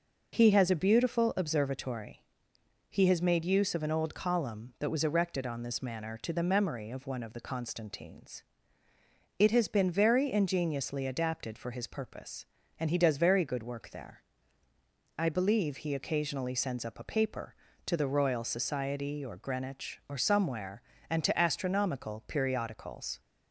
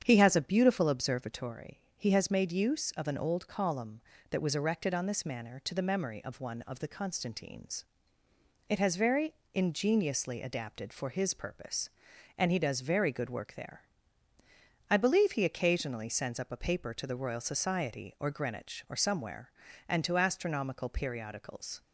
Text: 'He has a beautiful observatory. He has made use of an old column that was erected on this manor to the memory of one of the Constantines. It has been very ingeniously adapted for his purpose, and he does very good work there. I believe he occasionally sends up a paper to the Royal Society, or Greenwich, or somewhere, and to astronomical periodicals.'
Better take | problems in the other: first | starts louder than the rest; strong; until 1.0 s; 8 dB // skips "been"; at 8.9 s // pauses between "very" and "ingeniously"; slight; at 9.3 s; 0.22 s long

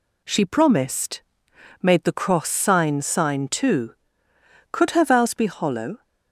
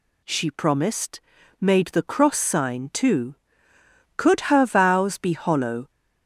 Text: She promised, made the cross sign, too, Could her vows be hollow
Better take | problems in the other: second | says "sign" twice; at 3.0 s

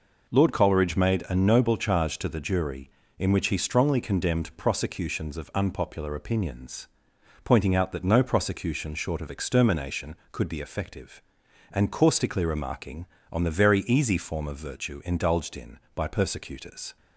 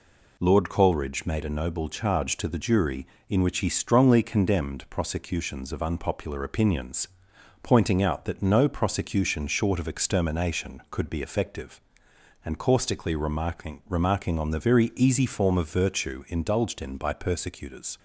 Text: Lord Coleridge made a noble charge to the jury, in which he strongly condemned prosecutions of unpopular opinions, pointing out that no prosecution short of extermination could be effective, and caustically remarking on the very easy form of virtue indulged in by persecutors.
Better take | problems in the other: first | says "remarking" twice; at 13.8 s

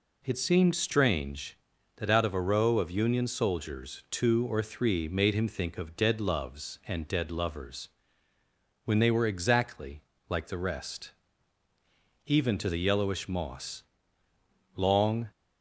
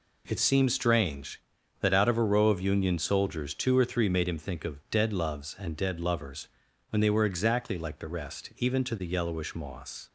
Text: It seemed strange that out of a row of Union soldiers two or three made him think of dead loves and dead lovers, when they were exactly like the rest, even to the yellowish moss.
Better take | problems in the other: second | pauses between "exactly" and "like"; slight; at 10.0 s; 0.26 s long // goes on to say "Long"; from 14.7 s on; 0.54 s long

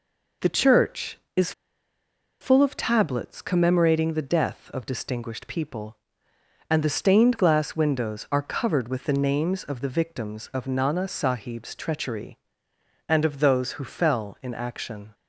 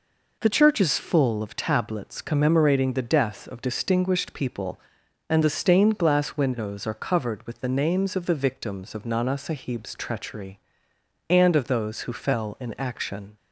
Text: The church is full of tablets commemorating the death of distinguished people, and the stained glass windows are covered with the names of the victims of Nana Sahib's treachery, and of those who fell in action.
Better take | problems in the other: second | pauses between "is" and "full"; noticeable; at 1.5 s; 0.89 s long

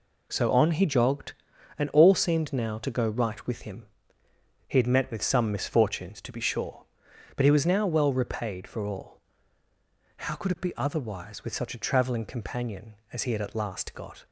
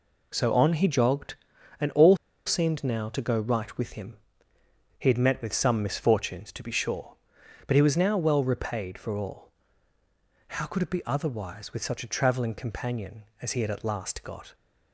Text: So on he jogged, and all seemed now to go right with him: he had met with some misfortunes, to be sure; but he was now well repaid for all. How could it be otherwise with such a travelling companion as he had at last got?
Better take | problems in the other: first | pauses between "all" and "seemed"; slight; at 2.1 s; 0.29 s long

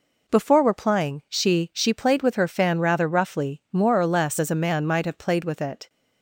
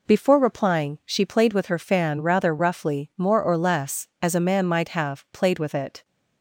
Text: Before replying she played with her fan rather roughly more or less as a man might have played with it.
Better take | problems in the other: second | says "she" twice; at 1.7 s

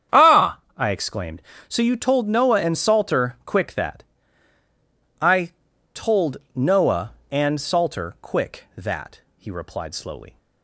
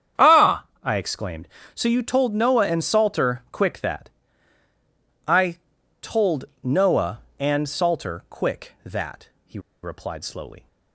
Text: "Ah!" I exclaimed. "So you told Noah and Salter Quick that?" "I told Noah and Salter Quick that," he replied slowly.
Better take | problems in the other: first | starts louder than the rest; strong; until 1.3 s; 8.5 dB; strong in the first // pauses between "I" and "told"; at 5.5 s; 0.42 s long; also in the first // pauses between "told" and "Noah"; slight; at 6.4 s; 0.18 s long; slight in the first // pauses between "he" and "replied"; slight; at 9.5 s; 0.23 s long

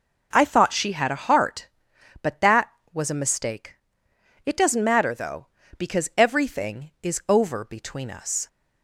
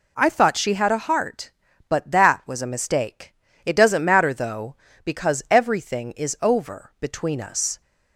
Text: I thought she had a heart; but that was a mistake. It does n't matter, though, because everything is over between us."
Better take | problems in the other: neither | none

